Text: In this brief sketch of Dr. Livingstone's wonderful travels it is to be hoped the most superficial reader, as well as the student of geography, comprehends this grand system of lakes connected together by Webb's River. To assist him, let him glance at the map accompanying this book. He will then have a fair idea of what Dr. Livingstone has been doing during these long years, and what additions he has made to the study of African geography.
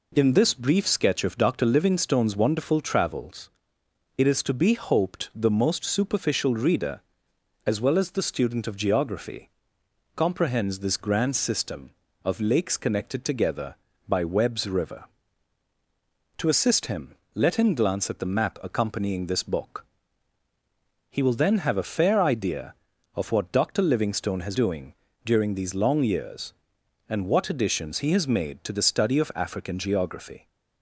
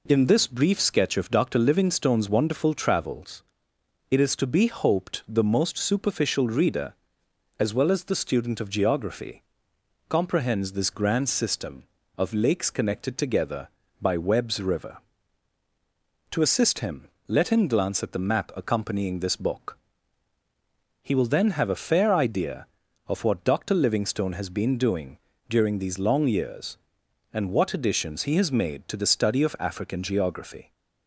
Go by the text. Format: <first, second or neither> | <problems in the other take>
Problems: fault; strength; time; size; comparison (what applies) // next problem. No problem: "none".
second | pauses between "travels" and "it"; noticeable; at 3.4 s; 0.66 s long; noticeable in the second // skips "been"; at 24.5 s // pauses between "doing" and "during"; slight; at 24.9 s; 0.32 s long; slight in the second